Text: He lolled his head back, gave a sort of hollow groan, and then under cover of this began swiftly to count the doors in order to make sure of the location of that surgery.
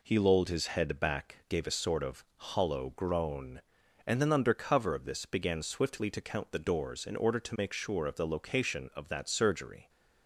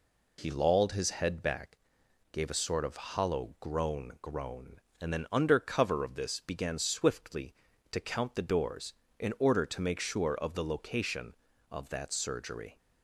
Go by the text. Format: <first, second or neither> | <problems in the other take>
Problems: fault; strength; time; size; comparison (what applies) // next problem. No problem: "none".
first | says "groan" twice; at 4.2 s